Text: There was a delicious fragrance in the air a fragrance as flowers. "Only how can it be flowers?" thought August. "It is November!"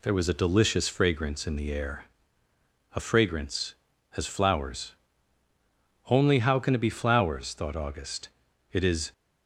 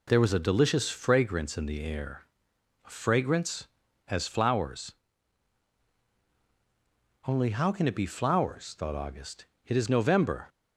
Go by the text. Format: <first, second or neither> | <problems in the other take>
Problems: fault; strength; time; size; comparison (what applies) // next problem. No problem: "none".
second | pauses between "air" and "a"; noticeable; at 2.0 s; 0.86 s long; noticeable in the second // stops before "November"; at 9.1 s